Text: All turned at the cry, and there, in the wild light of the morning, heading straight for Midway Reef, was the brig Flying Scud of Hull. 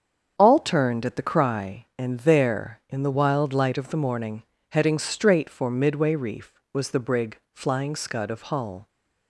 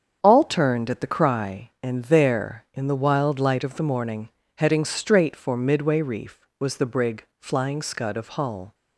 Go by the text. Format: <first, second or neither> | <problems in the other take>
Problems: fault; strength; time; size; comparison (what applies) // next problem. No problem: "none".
neither | starts louder than the rest; strong; the same in both // pauses between "brig" and "Flying"; slight; the same in both